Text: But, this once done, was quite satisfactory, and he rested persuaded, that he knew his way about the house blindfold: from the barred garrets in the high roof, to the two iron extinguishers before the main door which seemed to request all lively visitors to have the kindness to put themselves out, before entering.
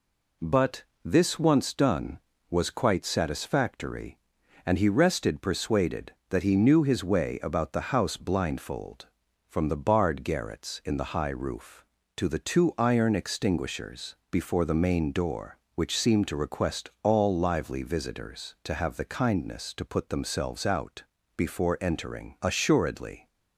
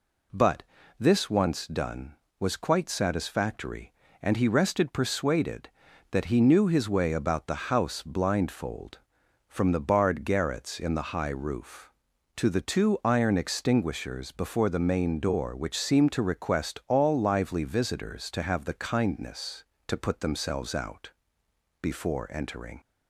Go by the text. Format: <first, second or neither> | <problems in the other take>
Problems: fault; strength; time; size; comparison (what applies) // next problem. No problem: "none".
second | pauses between "extinguishers" and "before"; slight; at 14.1 s; 0.16 s long // goes on to say "Assuredly"; noticeable; from 22.4 s on; 0.84 s long